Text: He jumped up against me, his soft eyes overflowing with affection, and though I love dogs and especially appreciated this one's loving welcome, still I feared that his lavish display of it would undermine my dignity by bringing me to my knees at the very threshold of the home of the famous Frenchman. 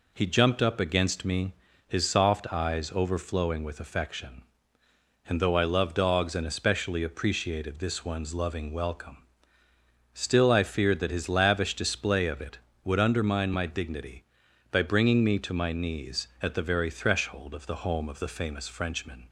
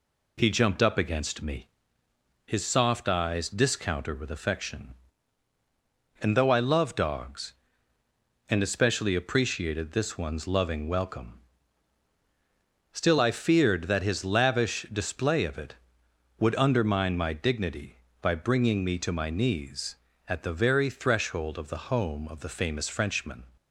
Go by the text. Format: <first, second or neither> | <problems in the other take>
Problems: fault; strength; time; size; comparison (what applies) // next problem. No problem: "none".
first | says "discounter" for "overflowing"; at 3.4 s